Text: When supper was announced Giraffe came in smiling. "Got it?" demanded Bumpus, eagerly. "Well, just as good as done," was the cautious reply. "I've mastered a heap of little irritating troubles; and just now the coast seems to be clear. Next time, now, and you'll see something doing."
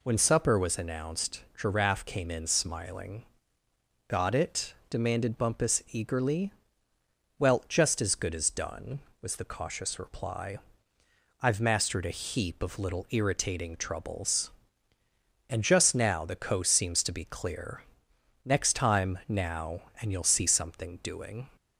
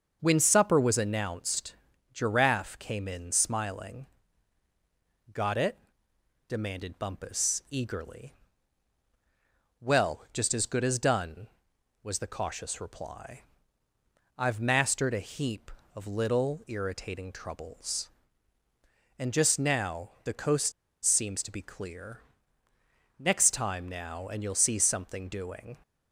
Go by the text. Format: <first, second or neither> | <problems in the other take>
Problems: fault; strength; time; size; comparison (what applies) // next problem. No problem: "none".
first | starts louder than the rest; until 1.2 s; 6.5 dB // pauses between "announced" and "Giraffe"; at 1.7 s; 0.40 s long // pauses between "coast" and "seems"; slight; at 20.7 s; 0.32 s long